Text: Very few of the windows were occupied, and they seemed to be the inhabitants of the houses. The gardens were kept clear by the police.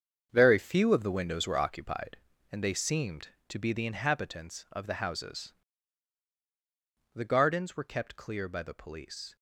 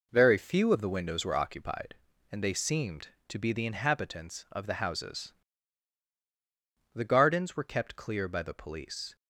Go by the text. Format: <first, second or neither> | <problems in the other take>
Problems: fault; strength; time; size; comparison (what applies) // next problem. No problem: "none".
second | gets quieter; strong; throughout; 11 dB